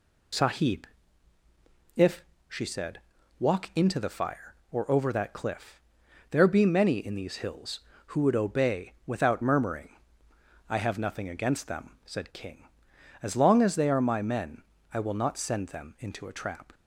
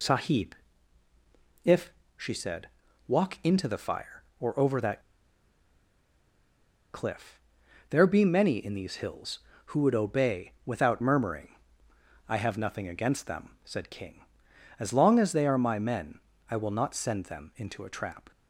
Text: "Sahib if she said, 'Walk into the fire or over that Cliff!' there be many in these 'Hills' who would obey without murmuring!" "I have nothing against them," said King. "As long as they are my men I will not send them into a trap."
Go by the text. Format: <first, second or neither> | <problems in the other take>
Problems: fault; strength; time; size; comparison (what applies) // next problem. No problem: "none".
first | pauses between "Sahib" and "if"; at 0.5 s; 1.0 s long; also in the first // pauses between "if" and "she"; slight; at 1.9 s; 0.24 s long; slight in the first // pauses between "that" and "Cliff"; strong; at 4.9 s; 1.9 s long // pauses between "men" and "I"; slight; at 16.1 s; 0.30 s long; slight in the first